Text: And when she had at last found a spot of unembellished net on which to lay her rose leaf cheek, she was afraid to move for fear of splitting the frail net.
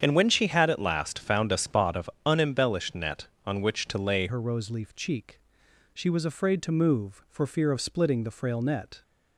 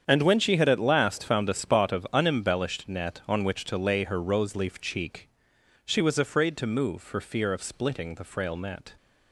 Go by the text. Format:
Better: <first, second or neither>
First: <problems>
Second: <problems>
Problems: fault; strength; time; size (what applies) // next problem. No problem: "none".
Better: second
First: starts louder than the rest; strong; until 1.0 s; 8 dB // pauses between "of" and "unembellished"; slight; at 2.0 s; 0.16 s long // changes voice at "her"; from 4.2 s on; 4.8 s long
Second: starts louder than the rest; strong; until 1.0 s; 8 dB